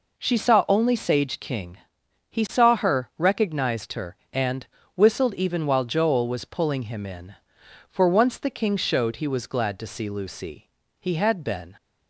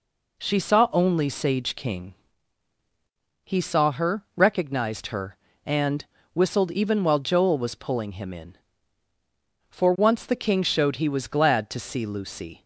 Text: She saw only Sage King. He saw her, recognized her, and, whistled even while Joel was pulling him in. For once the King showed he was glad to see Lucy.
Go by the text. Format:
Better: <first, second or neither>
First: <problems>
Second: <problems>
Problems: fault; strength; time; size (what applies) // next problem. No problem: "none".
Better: second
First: goes on to say "He had been"; noticeable; from 10.9 s on; 0.76 s long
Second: none